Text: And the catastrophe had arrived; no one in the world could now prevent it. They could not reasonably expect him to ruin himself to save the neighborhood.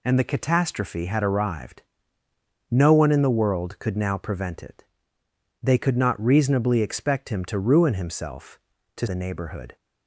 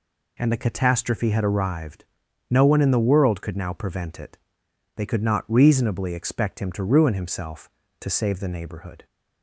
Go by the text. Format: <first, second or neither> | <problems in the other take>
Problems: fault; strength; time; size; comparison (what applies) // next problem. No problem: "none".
second | skips "save"; at 9.0 s